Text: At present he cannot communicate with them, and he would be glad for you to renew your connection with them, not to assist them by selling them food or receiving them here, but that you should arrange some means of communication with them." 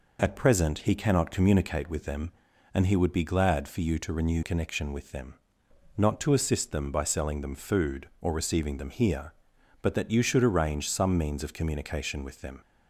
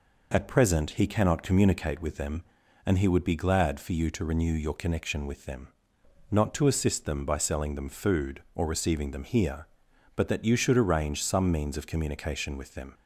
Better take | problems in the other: second | skips "your"; at 4.4 s

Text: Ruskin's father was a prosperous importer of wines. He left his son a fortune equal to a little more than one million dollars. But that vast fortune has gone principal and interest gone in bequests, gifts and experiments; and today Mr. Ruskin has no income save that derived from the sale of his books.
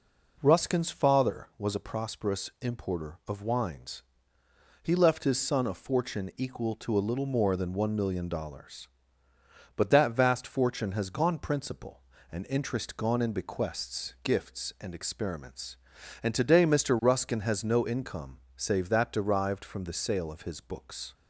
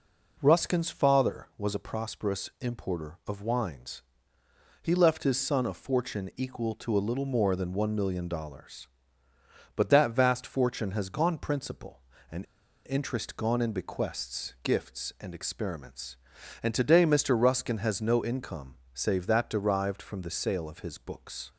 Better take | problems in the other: first | pauses between "and" and "interest"; at 12.4 s; 0.43 s long // pauses between "income" and "save"; slight; at 18.7 s; 0.16 s long; slight in the first

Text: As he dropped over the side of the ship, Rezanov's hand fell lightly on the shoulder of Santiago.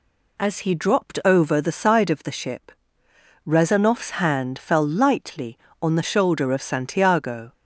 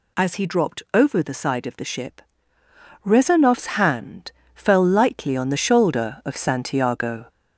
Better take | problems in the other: first | gets louder; slight; throughout; 3 dB // pauses between "hand" and "fell"; slight; at 4.3 s; 0.22 s long

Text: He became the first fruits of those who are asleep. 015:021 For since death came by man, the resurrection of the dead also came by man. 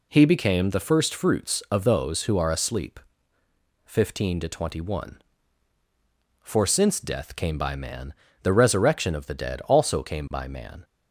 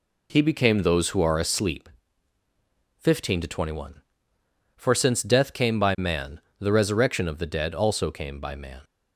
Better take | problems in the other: first | skips "the first fruits of"; at 0.8 s

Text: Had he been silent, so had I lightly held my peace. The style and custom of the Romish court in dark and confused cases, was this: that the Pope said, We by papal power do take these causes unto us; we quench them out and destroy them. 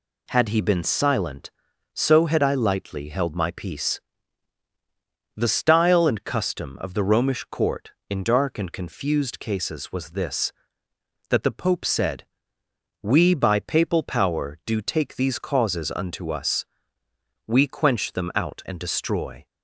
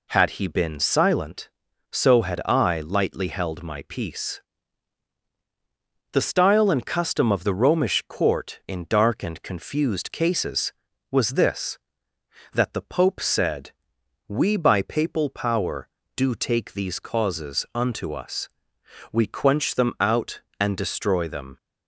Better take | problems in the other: second | stops before "them"; at 19.4 s

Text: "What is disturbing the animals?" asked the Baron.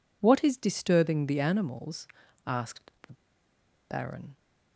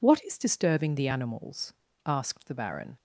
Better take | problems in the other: second | pauses between "asked" and "the"; slight; at 2.9 s; 0.16 s long // pauses between "the" and "Baron"; noticeable; at 3.1 s; 0.76 s long

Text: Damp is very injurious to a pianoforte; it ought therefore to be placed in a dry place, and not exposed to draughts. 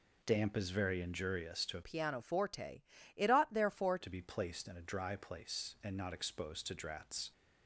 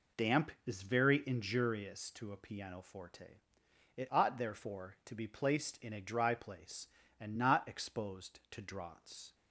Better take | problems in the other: second | changes voice from "pianoforte" to "therefore"; from 1.8 to 3.9 s; 2.1 s long

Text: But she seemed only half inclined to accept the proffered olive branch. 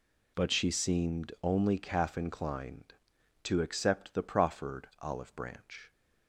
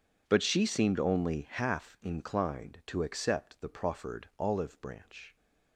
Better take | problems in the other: second | says "calf" for "half"; at 1.7 s

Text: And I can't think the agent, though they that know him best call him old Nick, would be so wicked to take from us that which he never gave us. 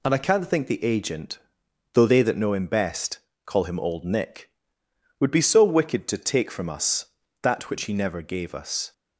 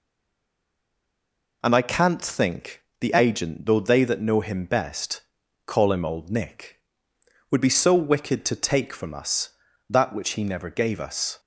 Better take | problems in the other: first | stays silent before the first word; noticeable; until 1.6 s; 1.6 s long // pauses between "think" and "the"; slight; at 2.8 s; 0.18 s long // pauses between "best" and "call"; at 5.2 s; 0.44 s long; slight in the first

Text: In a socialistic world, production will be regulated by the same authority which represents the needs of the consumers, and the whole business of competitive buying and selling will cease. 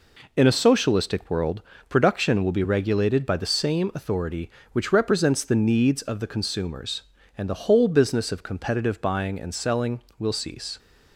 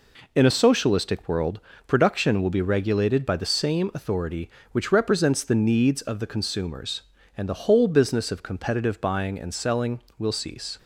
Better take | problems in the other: neither | none

